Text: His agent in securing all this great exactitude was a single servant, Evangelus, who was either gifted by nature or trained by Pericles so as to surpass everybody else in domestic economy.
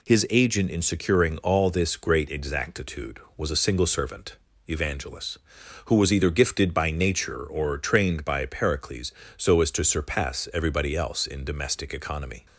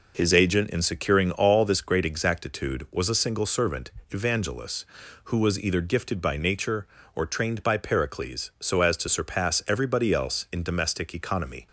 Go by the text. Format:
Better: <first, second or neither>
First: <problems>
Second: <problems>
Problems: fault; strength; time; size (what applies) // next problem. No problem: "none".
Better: neither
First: none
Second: none